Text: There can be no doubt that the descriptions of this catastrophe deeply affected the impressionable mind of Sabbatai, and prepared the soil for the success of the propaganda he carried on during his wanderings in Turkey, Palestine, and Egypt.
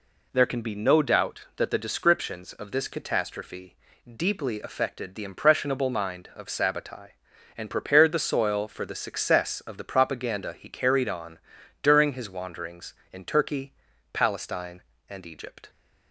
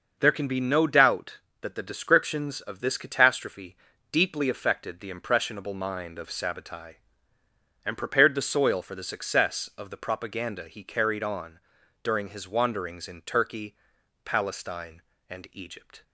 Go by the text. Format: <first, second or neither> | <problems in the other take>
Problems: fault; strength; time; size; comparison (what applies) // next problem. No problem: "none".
neither | pauses between "catastrophe" and "deeply"; the same in both // pauses between "on" and "during"; the same in both